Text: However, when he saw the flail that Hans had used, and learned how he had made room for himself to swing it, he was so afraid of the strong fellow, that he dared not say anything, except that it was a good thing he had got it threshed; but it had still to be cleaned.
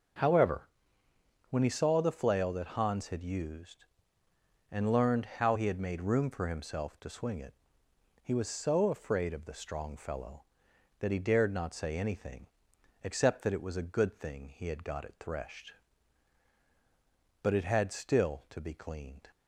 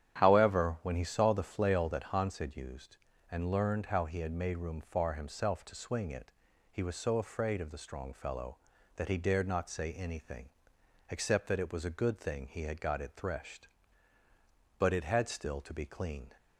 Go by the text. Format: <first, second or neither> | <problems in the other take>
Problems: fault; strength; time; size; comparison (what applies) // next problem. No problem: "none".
first | starts louder than the rest; strong; until 1.1 s; 9.5 dB; noticeable in the first // says "far" for "for"; at 4.8 s